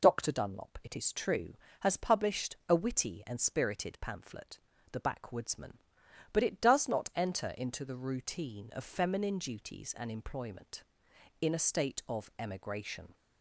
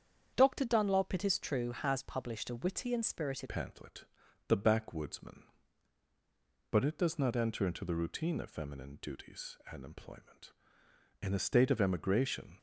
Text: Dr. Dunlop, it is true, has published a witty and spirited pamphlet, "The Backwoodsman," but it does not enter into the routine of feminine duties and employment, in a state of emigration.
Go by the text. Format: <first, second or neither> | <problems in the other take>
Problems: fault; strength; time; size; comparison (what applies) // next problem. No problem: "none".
first | starts louder than the rest; strong; until 1.3 s; 8 dB // changes voice at "pamphlet"; from 3.4 s on; 9.1 s long